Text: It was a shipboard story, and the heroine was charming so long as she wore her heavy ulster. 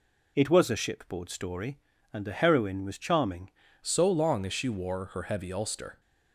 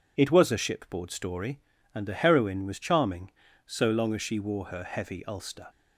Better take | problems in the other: second | changes voice at "so"; from 3.8 s on; 2.1 s long

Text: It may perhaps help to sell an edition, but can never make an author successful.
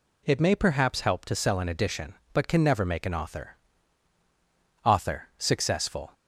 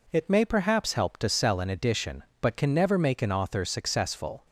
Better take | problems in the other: second | says "author" twice; at 4.8 s

